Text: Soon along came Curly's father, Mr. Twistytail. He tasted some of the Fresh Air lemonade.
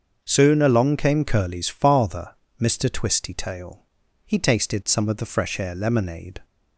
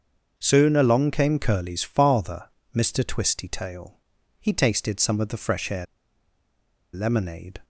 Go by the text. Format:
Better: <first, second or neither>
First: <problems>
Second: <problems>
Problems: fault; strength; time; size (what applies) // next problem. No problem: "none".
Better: first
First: starts louder than the rest; until 1.2 s; 6.5 dB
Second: starts louder than the rest; until 1.3 s; 6.5 dB // pauses between "Air" and "lemonade"; at 5.8 s; 1.0 s long